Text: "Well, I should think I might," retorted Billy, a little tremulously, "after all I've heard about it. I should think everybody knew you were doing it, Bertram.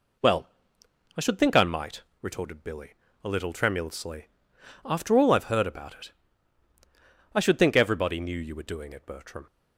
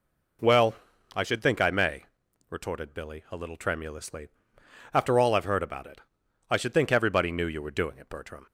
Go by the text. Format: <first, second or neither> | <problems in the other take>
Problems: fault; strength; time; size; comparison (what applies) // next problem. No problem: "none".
first | says "may" for "might"; at 1.6 s